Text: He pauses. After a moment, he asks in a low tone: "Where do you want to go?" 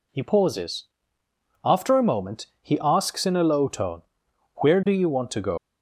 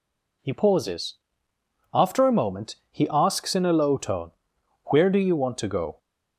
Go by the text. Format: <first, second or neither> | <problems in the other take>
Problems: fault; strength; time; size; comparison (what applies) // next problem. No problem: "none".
second | leaves "go" unfinished; at 5.5 s; 135 ms